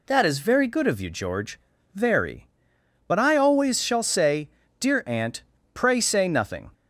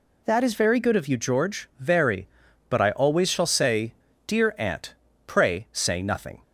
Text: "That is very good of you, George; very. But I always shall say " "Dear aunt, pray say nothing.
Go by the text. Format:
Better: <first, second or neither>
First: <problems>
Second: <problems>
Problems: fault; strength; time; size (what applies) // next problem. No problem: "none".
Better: neither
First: none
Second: none